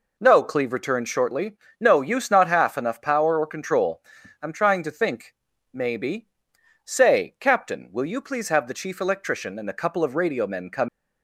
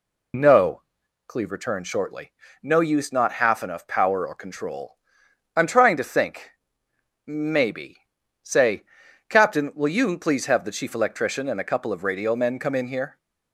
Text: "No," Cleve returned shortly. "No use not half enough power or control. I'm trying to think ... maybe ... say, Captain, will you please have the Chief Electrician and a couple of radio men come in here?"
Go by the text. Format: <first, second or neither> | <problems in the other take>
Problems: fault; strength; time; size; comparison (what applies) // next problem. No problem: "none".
second | stops before "in here"; at 10.8 s